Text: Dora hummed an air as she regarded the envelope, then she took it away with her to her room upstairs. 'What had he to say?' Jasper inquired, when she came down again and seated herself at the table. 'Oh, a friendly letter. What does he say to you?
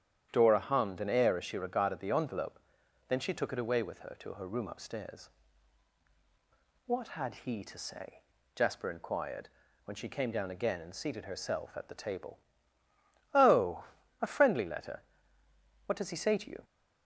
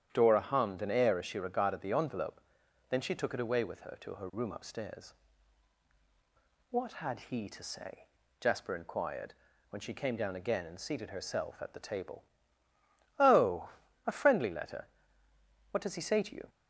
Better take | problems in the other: neither | starts louder than the rest; strong; the same in both

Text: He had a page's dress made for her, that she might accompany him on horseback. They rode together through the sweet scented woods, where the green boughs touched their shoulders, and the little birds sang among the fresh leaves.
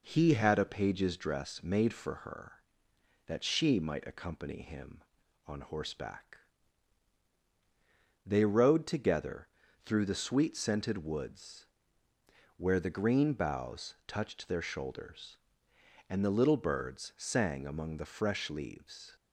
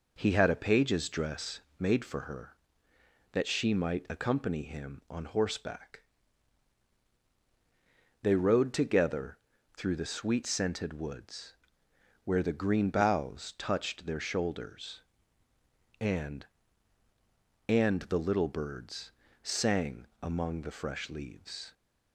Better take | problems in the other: first | pauses between "dress" and "made"; slight; at 1.5 s; 0.20 s long // pauses between "together" and "through"; at 9.3 s; 0.38 s long; also in the first // says "and" twice; at 17.6 s // pauses between "birds" and "sang"; slight; at 19.1 s; 0.32 s long // pauses between "sang" and "among"; slight; at 20.0 s; 0.16 s long

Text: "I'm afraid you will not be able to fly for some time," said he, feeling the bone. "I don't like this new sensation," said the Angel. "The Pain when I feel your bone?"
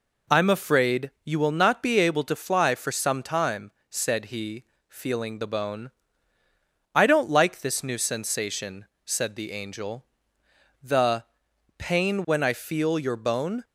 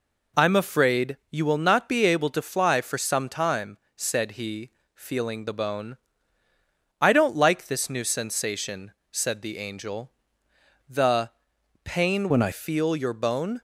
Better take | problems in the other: first | pauses between "The" and "Pain"; noticeable; at 11.2 s; 0.54 s long; noticeable in the first // changes voice from "when" to "I"; from 12.3 to 12.5 s; 0.2 s long

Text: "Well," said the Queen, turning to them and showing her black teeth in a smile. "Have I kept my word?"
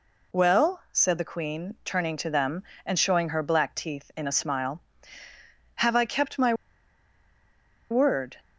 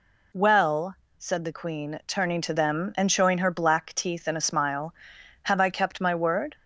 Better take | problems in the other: second | pauses between "my" and "word"; strong; at 6.5 s; 1.3 s long

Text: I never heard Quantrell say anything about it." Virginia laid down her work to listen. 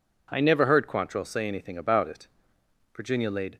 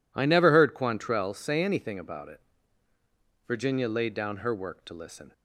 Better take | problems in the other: second | stops before "down her work to listen"; at 3.5 s

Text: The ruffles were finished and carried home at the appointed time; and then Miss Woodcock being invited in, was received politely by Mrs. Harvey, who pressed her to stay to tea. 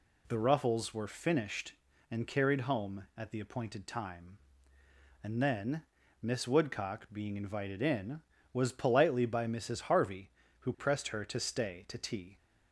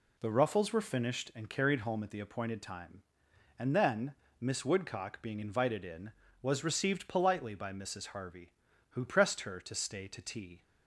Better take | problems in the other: second | pauses between "then" and "Miss"; slight; at 5.8 s; 0.36 s long; slight in the second // skips "received"; at 8.7 s

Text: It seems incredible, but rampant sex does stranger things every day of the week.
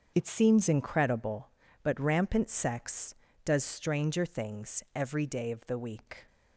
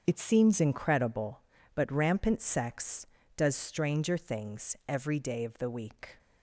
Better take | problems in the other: neither | starts louder than the rest; strong; the same in both

